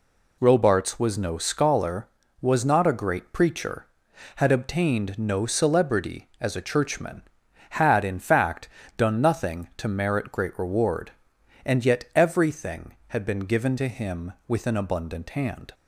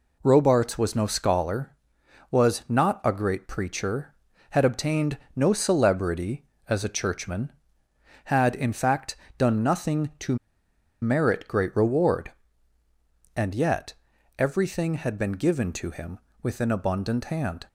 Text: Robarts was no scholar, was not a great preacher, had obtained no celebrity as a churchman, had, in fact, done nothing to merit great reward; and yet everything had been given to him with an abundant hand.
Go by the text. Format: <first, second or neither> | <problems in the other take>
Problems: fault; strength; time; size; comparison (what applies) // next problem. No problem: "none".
first | pauses between "obtained" and "no"; slight; at 5.1 s; 0.16 s long // pauses between "to" and "merit"; noticeable; at 10.3 s; 0.66 s long // pauses between "yet" and "everything"; at 13.9 s; 0.44 s long